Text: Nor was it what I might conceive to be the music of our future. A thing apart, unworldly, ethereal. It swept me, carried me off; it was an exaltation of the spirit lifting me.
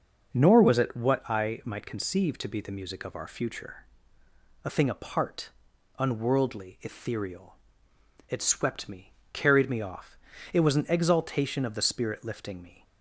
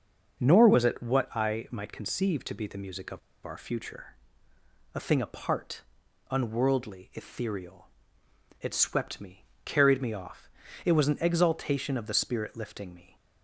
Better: first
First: starts louder than the rest; noticeable; until 1.3 s; 6 dB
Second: starts louder than the rest; noticeable; until 1.4 s; 6 dB // pauses between "of" and "our"; slight; at 3.1 s; 0.25 s long

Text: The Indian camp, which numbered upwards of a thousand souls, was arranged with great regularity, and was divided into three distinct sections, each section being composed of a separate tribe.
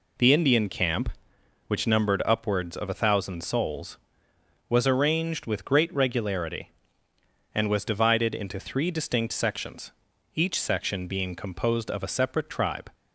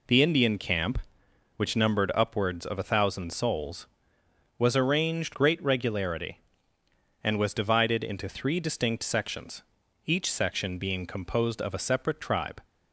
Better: first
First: none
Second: skips "with"; at 5.3 s

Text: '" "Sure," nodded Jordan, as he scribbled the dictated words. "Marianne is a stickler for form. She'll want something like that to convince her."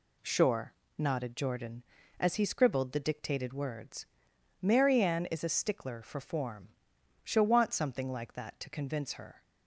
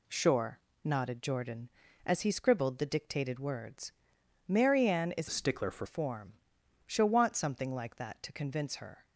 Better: first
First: none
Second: changes voice from "a" to "for"; from 5.2 to 5.8 s; 0.6 s long

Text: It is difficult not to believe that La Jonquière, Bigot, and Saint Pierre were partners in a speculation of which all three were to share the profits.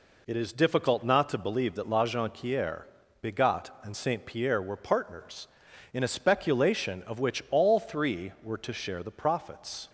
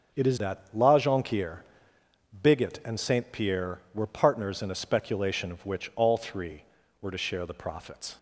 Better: first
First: none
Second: starts louder than the rest; until 1.2 s; 7 dB // skips "difficult not to believe"; at 0.3 s

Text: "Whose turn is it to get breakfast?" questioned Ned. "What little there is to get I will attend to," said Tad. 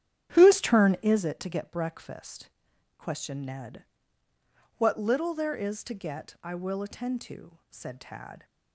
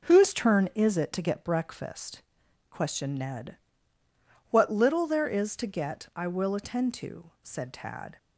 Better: second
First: starts louder than the rest; strong; until 1.3 s; 10.5 dB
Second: none

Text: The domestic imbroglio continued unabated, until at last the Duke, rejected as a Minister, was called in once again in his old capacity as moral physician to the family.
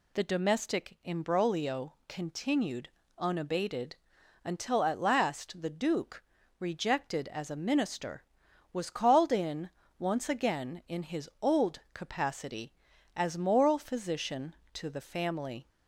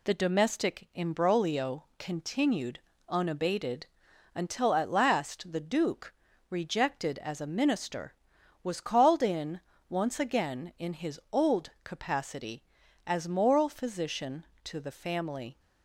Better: first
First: pauses between "imbroglio" and "continued"; slight; at 1.9 s; 0.16 s long // pauses between "continued" and "unabated"; slight; at 2.8 s; 0.28 s long // pauses between "in" and "once"; slight; at 9.6 s; 0.30 s long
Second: gets quieter; noticeable; throughout; 4 dB // pauses between "imbroglio" and "continued"; slight; at 1.8 s; 0.16 s long // pauses between "continued" and "unabated"; slight; at 2.7 s; 0.28 s long // pauses between "in" and "once"; slight; at 9.5 s; 0.30 s long

